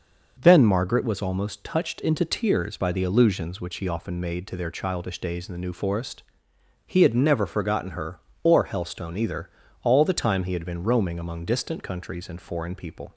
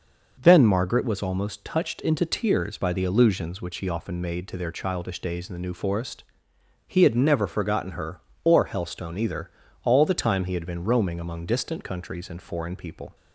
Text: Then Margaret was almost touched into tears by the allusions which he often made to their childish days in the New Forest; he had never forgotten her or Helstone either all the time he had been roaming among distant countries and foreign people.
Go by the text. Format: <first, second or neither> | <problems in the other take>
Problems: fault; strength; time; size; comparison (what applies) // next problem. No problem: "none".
neither | pauses between "either" and "all"; slight; the same in both